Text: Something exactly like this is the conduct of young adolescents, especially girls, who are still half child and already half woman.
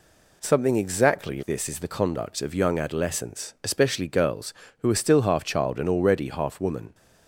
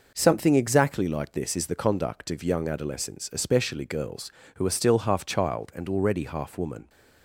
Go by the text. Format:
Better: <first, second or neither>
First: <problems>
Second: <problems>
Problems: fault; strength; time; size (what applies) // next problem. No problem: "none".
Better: second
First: skips "like"; at 1.4 s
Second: none